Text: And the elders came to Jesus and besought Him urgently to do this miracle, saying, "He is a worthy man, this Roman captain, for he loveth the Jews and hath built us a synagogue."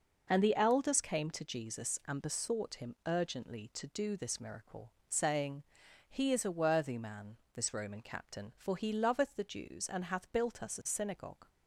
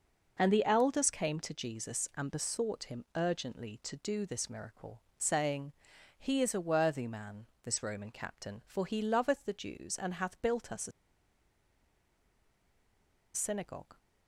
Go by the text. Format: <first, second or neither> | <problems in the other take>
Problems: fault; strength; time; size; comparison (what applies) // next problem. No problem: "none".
first | pauses between "a" and "synagogue"; strong; at 10.9 s; 2.4 s long